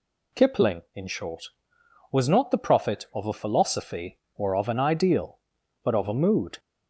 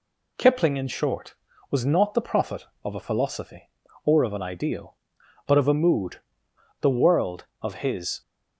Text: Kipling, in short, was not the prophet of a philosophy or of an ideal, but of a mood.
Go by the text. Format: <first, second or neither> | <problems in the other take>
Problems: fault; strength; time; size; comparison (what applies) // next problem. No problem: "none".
first | goes on to say "The world of his"; from 6.8 s on; 1.4 s long